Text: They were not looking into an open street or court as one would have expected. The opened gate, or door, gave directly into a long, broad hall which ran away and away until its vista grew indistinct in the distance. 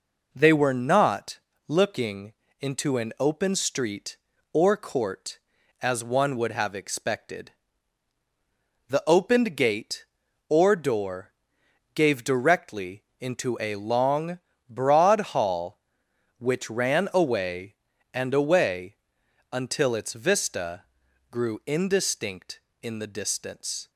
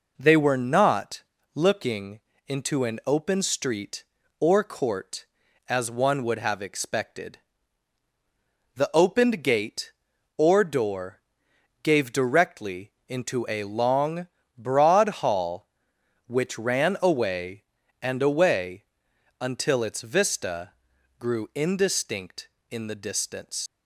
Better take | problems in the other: first | pauses between "not" and "looking"; slight; at 1.2 s; 0.31 s long; slight in the first // pauses between "looking" and "into"; slight; at 2.2 s; 0.26 s long; slight in the first // pauses between "away" and "until"; noticeable; at 18.8 s; 0.56 s long; noticeable in the first // pauses between "vista" and "grew"; noticeable; at 20.7 s; 0.46 s long; noticeable in the first // leaves "distance" unfinished; at 23.6 s; 120 ms

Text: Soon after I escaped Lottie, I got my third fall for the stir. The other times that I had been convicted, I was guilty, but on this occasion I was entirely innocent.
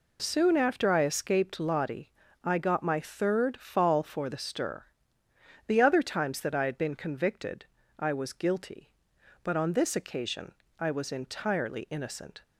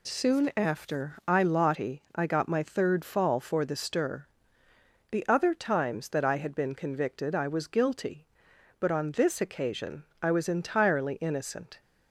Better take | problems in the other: first | skips "escaped"; at 1.4 s // pauses between "occasion" and "I"; slight; at 10.0 s; 0.18 s long; slight in the first

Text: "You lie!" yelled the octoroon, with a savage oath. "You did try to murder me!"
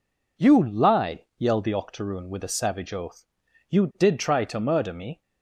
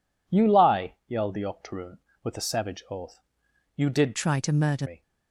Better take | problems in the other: first | changes voice from "try" to "murder"; from 4.1 to 4.8 s; 0.7 s long

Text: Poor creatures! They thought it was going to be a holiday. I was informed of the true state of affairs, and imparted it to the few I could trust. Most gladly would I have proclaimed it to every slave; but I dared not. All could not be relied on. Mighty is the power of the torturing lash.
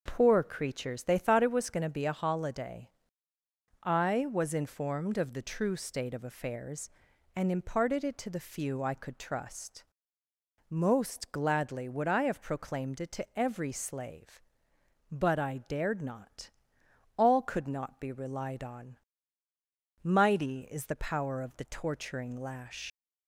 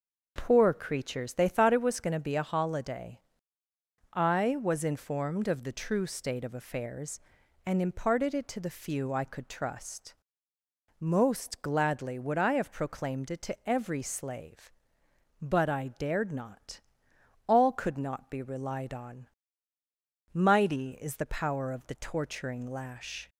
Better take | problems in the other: second | leaves "lash" unfinished; at 22.8 s; 85 ms

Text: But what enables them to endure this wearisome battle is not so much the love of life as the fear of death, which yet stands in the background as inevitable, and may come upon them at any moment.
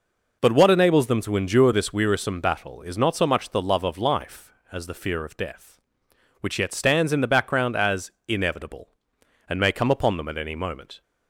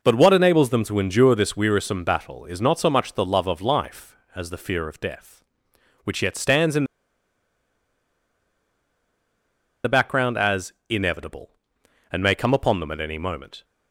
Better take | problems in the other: first | pauses between "in" and "the"; strong; at 6.8 s; 3.0 s long // pauses between "as" and "inevitable"; slight; at 10.7 s; 0.16 s long; slight in the first

